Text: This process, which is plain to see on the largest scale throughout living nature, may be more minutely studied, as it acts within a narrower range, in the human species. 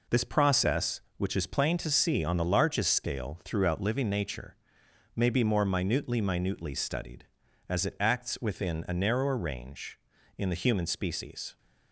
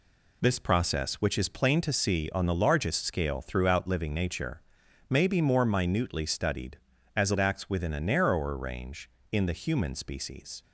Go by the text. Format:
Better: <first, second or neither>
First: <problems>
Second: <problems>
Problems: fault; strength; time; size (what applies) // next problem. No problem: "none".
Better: second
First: says "minutely" twice; at 6.2 s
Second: none